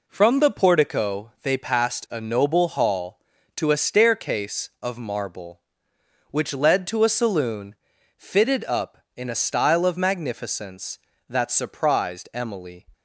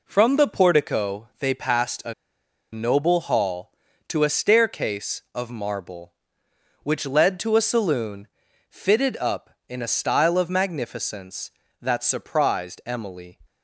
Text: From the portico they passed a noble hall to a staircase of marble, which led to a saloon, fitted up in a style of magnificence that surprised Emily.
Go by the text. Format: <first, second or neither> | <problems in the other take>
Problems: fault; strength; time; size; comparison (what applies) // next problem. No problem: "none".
first | pauses between "a" and "noble"; noticeable; at 2.1 s; 0.59 s long